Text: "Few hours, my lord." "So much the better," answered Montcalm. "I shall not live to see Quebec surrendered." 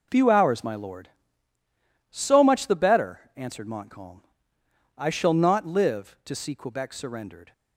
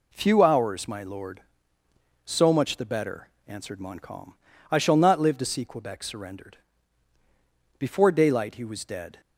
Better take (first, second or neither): first